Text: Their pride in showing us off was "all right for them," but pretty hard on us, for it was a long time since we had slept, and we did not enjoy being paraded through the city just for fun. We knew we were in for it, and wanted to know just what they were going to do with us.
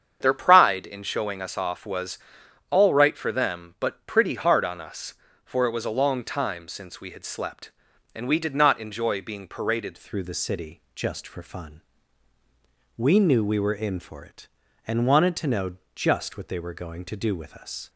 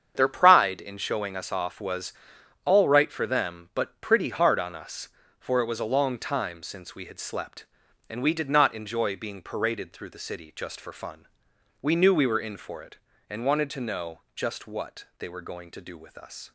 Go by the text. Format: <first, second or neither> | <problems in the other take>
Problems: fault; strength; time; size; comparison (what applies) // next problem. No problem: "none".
second | starts louder than the rest; strong; until 1.2 s; 8 dB; strong in the second // pauses between "was" and "all"; noticeable; at 2.1 s; 0.50 s long; noticeable in the second // changes voice at "through"; from 9.9 s on; 7.9 s long // pauses between "know" and "just"; slight; at 15.7 s; 0.18 s long; slight in the second